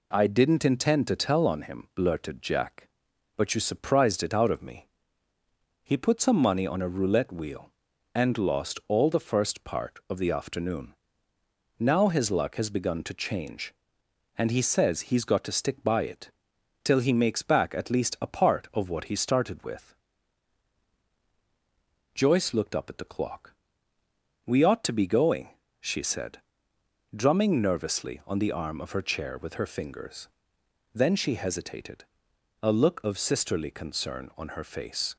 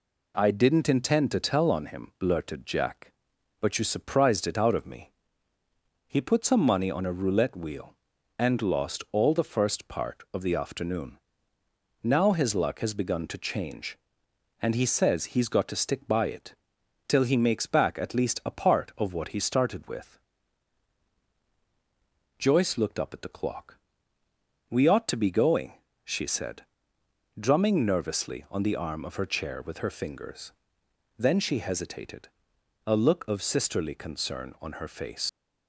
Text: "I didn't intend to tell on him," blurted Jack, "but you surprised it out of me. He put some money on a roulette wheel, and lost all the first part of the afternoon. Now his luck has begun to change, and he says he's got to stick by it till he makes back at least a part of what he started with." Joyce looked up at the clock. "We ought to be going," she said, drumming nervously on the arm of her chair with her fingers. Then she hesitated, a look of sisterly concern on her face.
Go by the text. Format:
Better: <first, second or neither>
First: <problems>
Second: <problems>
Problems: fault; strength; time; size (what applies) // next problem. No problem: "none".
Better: first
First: pauses between "it" and "till"; noticeable; at 16.2 s; 0.54 s long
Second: pauses between "it" and "till"; noticeable; at 16.5 s; 0.54 s long // leaves "face" unfinished; at 35.2 s; 100 ms